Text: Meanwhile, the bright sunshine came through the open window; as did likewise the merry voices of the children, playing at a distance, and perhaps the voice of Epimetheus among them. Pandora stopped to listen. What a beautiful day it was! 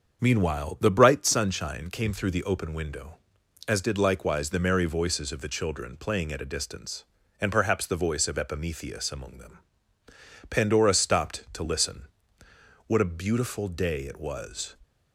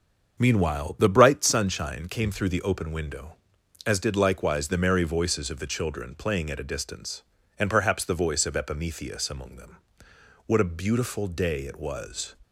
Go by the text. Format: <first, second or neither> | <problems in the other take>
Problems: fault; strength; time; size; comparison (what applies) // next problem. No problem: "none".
first | starts louder than the rest; until 1.4 s; 7 dB; also in the first // skips "Pandora stopped to listen"; at 10.1 s